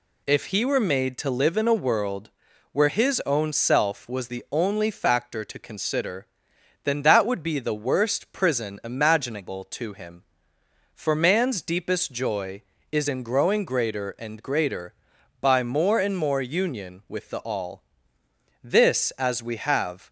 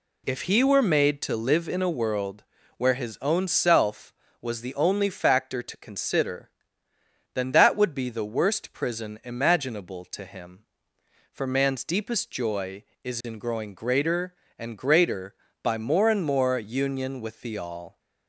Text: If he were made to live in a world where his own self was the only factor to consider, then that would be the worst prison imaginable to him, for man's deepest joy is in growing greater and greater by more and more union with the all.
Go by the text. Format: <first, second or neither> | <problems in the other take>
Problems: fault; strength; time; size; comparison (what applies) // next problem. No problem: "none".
second | pauses between "world" and "where"; at 2.2 s; 0.42 s long; slight in the second // goes on to say "This as we have"; from 18.6 s on; 1.4 s long